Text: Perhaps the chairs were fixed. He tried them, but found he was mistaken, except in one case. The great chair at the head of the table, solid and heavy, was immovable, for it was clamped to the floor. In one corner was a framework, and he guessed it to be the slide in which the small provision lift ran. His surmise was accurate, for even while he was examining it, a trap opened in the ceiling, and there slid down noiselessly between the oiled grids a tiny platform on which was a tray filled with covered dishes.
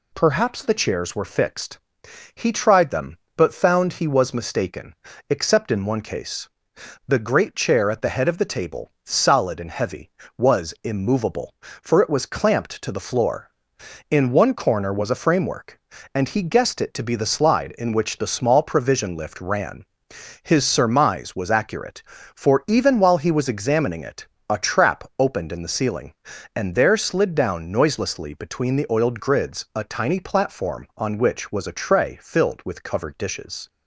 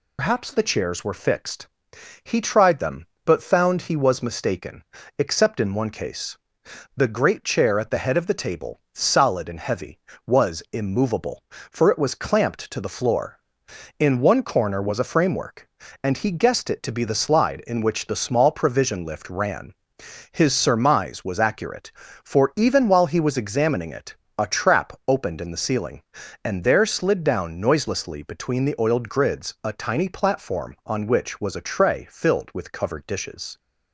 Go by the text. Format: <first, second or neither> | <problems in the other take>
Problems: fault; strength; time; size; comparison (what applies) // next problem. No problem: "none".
first | loses the start of "Perhaps"; at 0.1 s; 155 ms